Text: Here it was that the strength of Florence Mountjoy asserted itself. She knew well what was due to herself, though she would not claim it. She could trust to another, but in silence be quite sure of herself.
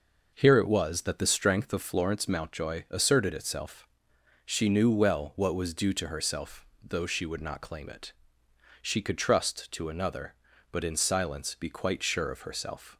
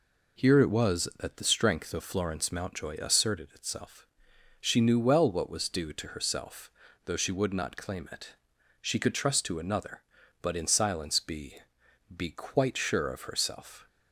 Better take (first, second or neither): first